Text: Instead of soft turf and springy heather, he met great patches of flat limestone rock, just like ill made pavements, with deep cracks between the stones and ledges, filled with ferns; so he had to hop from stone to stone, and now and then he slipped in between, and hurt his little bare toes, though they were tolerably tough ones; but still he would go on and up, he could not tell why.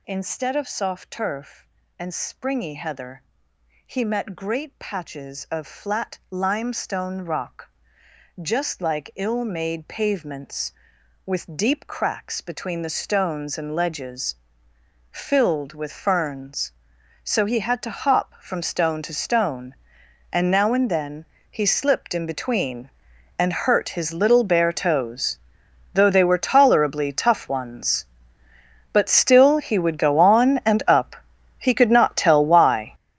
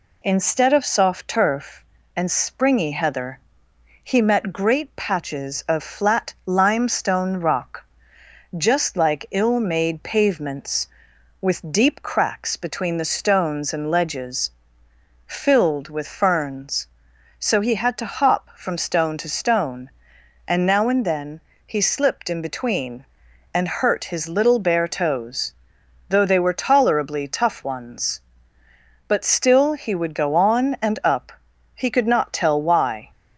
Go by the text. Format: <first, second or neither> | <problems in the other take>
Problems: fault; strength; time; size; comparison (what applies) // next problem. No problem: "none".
second | gets louder; strong; throughout; 13 dB // pauses between "then" and "he"; slight; at 21.2 s; 0.24 s long; slight in the second